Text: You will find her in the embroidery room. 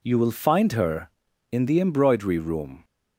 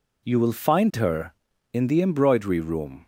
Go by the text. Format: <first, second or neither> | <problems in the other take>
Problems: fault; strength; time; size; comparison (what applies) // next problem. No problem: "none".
neither | none